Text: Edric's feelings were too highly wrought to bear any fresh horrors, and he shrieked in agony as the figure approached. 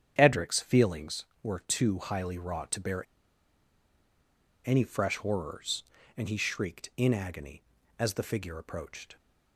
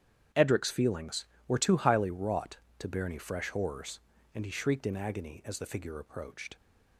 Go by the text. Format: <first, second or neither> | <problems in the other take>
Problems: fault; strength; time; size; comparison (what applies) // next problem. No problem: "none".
second | starts louder than the rest; strong; until 1.1 s; 9 dB; strong in the second // pauses between "bear" and "any"; strong; at 3.0 s; 1.6 s long